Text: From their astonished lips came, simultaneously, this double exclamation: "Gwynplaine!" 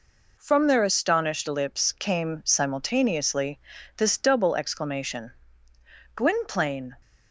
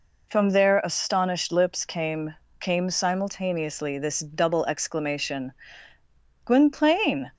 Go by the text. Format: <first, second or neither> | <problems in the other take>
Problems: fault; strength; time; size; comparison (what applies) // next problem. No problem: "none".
first | says "came" twice; at 2.5 s